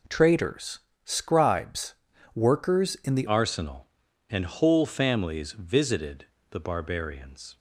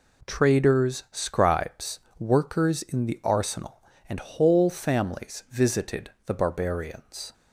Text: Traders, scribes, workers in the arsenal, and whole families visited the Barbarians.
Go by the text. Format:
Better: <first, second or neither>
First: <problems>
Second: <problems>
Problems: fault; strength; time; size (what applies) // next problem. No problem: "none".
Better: second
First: changes voice at "arsenal"; from 3.2 s on; 4.3 s long // pauses between "visited" and "the"; slight; at 6.2 s; 0.26 s long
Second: pauses between "visited" and "the"; slight; at 6.1 s; 0.16 s long